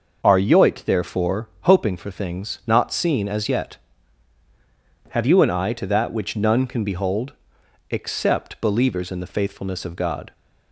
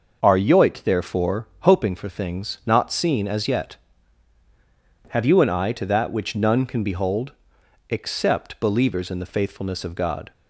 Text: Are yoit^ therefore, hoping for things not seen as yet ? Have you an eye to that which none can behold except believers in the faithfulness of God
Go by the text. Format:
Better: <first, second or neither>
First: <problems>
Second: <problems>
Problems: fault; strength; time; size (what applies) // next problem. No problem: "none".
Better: neither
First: pauses between "behold" and "except"; noticeable; at 7.3 s; 0.58 s long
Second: pauses between "behold" and "except"; noticeable; at 7.3 s; 0.58 s long